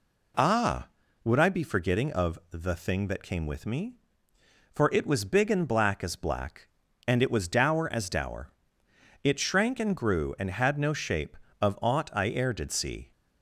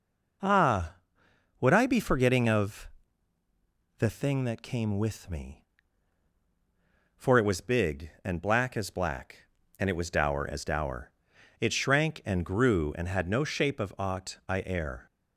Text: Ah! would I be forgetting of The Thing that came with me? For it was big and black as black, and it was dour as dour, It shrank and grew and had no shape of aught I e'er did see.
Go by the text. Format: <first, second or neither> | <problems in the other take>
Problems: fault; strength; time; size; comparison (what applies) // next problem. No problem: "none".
first | pauses between "of" and "The"; at 2.8 s; 1.1 s long // stops before "did see"; at 15.0 s